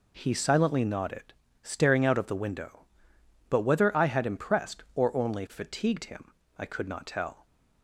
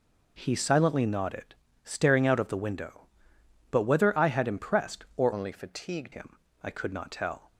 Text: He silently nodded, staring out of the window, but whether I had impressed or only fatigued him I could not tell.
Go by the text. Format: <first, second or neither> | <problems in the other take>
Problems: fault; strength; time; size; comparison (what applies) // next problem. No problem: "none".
first | changes voice from "only" to "fatigued"; from 5.3 to 6.1 s; 0.8 s long // pauses between "him" and "I"; slight; at 6.3 s; 0.26 s long; slight in the first